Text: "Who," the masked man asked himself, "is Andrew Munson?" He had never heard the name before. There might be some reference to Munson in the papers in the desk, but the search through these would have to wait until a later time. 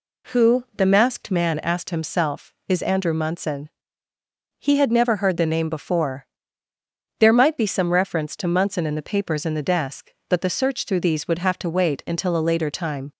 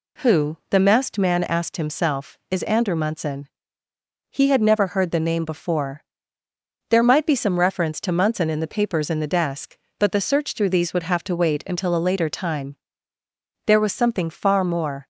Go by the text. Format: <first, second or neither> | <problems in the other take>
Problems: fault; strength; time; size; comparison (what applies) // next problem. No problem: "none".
first | goes on to say "There was something far more"; from 13.6 s on; 1.4 s long